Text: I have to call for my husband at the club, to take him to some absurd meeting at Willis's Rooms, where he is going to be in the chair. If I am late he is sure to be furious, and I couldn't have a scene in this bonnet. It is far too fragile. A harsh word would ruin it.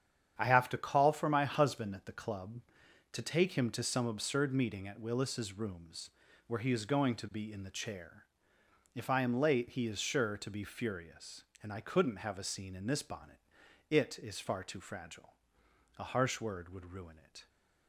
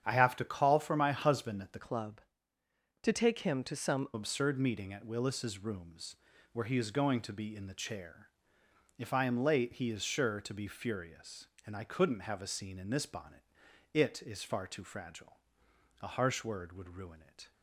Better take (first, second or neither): first